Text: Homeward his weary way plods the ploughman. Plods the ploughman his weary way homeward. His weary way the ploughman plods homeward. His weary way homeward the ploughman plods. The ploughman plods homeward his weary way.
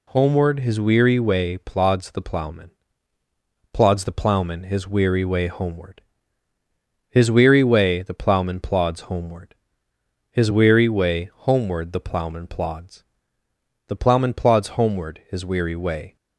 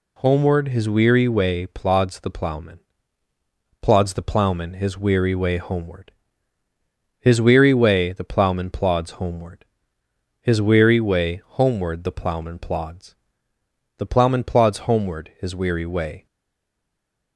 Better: first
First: none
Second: stays silent after the last word; from 16.2 s on; 1.1 s long

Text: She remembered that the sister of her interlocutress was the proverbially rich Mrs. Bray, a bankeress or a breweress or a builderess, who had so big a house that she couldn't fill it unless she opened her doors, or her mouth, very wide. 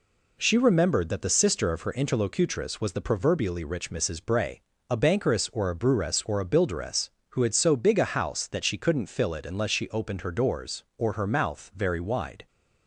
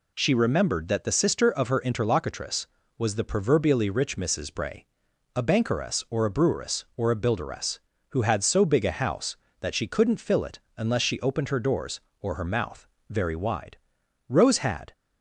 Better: first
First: none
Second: pauses between "it" and "unless"; slight; at 10.5 s; 0.18 s long // goes on to say "Rose had"; noticeable; from 14.2 s on; 0.64 s long

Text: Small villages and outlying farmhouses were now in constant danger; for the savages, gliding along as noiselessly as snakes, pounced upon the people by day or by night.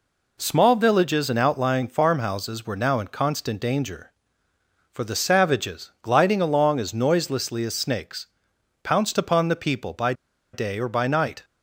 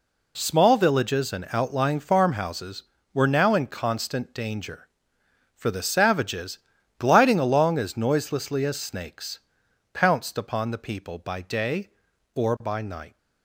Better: second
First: pauses between "by" and "day"; at 10.1 s; 0.40 s long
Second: none

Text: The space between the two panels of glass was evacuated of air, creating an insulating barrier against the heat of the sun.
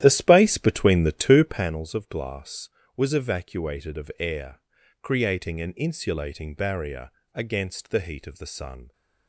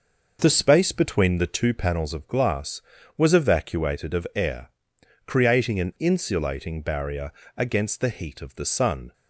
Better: second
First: starts louder than the rest; strong; until 1.8 s; 12 dB // pauses between "barrier" and "against"; slight; at 7.0 s; 0.24 s long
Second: pauses between "barrier" and "against"; slight; at 7.3 s; 0.26 s long

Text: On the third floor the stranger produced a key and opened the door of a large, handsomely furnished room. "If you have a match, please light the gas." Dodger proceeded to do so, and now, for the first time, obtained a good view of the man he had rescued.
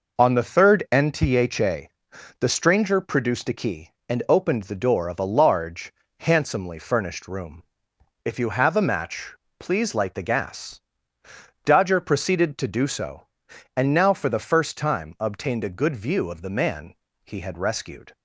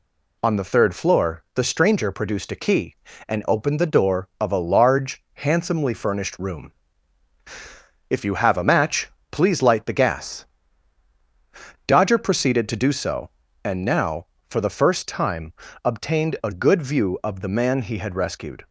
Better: second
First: says "ntha" for "floor"; at 0.9 s // pauses between "man" and "he"; slight; at 16.9 s; 0.32 s long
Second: none

